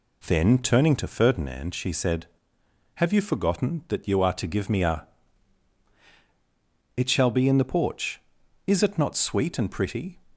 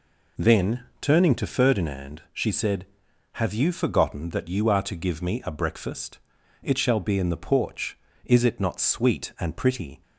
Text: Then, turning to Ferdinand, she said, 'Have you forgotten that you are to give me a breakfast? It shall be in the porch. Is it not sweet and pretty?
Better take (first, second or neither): second